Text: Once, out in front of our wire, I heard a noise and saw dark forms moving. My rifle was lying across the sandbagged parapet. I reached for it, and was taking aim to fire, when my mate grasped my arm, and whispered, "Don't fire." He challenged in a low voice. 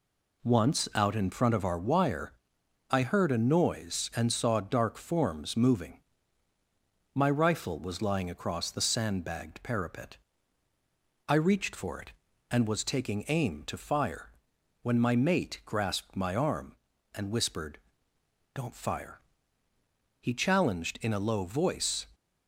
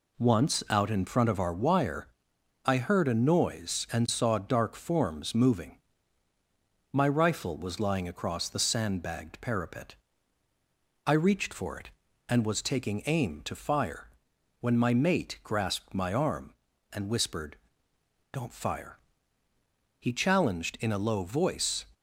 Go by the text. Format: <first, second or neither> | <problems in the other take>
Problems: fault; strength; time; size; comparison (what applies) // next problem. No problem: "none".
neither | none